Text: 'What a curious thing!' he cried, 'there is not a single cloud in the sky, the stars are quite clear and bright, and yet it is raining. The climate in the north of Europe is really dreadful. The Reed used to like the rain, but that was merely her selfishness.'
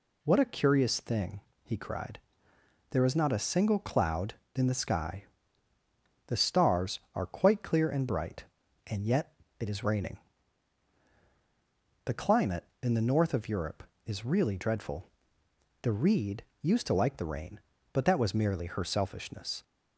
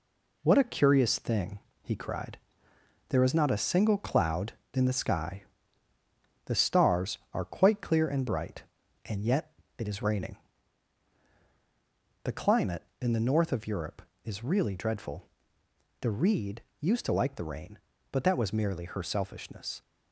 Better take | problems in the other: first | gets quieter; noticeable; throughout; 5 dB // pauses between "yet" and "it"; slight; at 9.5 s; 0.26 s long; slight in the first // pauses between "Reed" and "used"; slight; at 16.6 s; 0.18 s long; slight in the first

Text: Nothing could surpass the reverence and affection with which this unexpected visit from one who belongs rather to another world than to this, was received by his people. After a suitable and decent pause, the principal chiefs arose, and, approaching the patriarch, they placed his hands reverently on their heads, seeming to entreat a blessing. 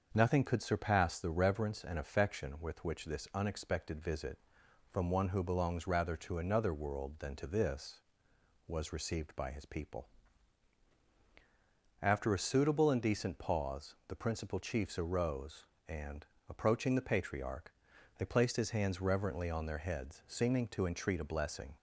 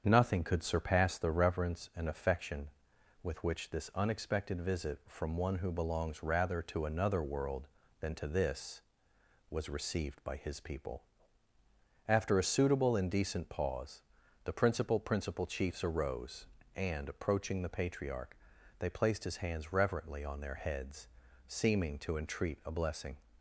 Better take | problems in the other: first | starts louder than the rest; strong; until 1.0 s; 7 dB; also in the first // says "principal" twice; at 14.9 s

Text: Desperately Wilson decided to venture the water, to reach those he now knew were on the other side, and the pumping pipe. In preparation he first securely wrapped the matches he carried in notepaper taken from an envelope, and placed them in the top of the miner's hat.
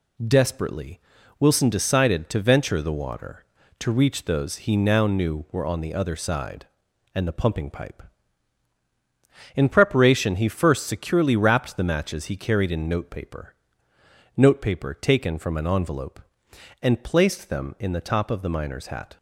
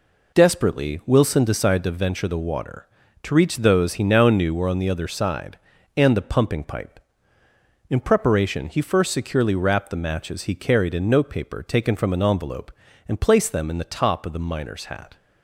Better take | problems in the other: second | pauses between "Desperately" and "Wilson"; at 0.9 s; 0.40 s long // says "notepaper" twice; at 14.3 s

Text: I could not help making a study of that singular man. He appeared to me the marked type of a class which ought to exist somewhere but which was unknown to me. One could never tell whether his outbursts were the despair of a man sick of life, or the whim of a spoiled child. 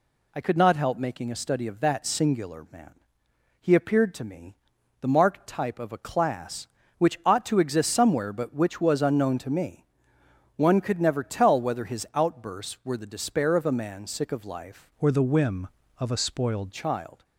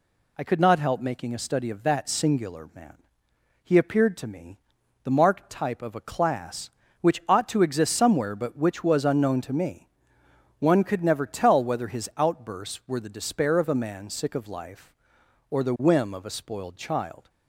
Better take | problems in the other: second | pauses between "me" and "the"; noticeable; at 4.5 s; 0.46 s long; noticeable in the second // changes voice from "or" to "spoiled"; from 14.9 to 16.7 s; 1.8 s long

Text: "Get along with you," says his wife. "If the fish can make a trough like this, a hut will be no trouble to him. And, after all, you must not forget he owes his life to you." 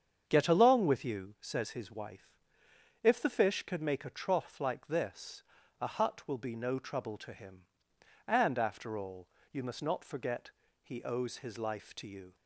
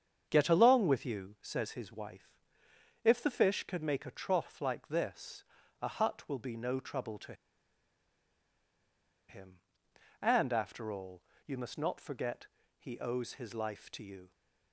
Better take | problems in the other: first | starts louder than the rest; strong; until 1.3 s; 7.5 dB; strong in the first // pauses between "to" and "him"; strong; at 7.3 s; 1.9 s long // pauses between "forget" and "he"; slight; at 12.4 s; 0.32 s long; slight in the first

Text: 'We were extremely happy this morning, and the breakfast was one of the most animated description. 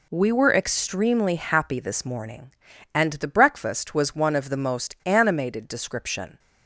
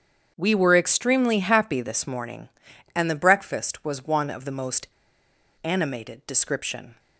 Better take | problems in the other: first | starts louder than the rest; strong; until 1.3 s; 8 dB // pauses between "most" and "animated"; noticeable; at 4.8 s; 0.74 s long

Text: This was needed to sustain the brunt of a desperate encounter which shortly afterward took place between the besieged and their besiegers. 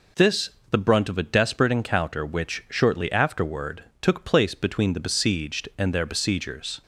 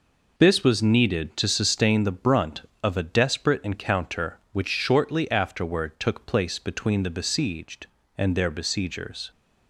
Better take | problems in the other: second | skips "was needed to sustain"; at 0.6 s // pauses between "afterward" and "took"; slight; at 3.8 s; 0.18 s long

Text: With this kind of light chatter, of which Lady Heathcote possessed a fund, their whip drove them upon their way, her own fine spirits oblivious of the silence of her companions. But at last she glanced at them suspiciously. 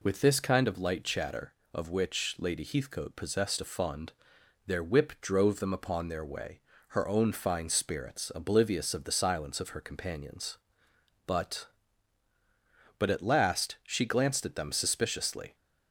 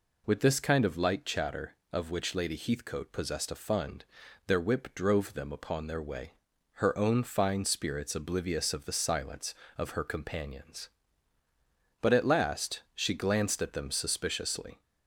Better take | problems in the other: second | says "But" twice; at 12.9 s

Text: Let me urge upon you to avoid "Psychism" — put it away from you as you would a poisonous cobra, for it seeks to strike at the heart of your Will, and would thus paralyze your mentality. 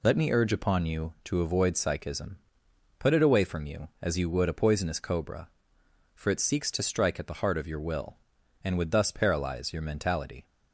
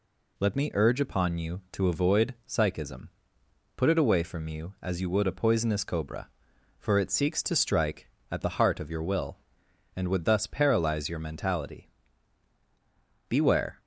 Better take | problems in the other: first | goes on to say "Beware"; from 13.2 s on; 0.50 s long

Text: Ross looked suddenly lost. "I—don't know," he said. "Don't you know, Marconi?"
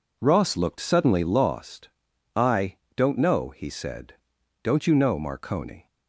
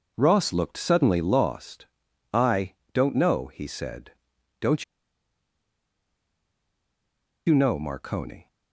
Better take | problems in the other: first | pauses between "Don't" and "you"; strong; at 4.8 s; 2.6 s long

